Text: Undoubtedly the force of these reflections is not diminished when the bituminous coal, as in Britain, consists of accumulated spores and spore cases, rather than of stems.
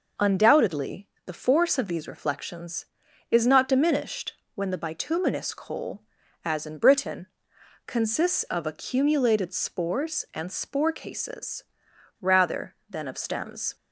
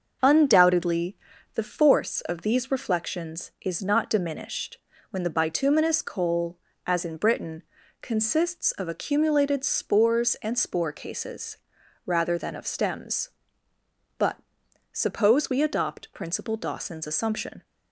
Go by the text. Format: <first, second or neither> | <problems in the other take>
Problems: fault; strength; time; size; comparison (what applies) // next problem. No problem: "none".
first | starts louder than the rest; until 1.6 s; 6.5 dB // pauses between "Undoubtedly" and "the"; at 1.1 s; 0.38 s long; slight in the first // pauses between "diminished" and "when"; slight; at 4.7 s; 0.32 s long; slight in the first // goes on to say "But suppose we adopt Principal Dawson's assumption"; strong; from 14.1 s on; 3.4 s long